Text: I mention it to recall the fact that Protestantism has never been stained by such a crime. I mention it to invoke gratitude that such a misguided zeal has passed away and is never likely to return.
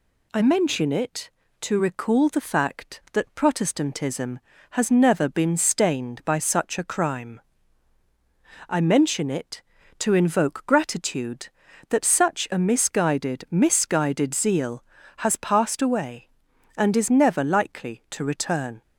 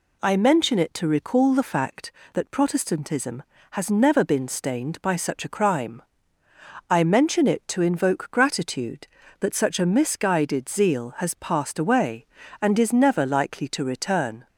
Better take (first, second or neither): second